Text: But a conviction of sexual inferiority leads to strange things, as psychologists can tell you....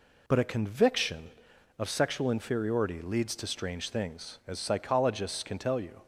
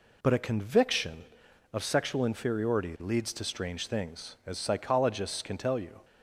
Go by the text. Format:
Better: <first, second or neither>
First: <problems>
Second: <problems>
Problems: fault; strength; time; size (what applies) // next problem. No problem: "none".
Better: neither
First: none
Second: none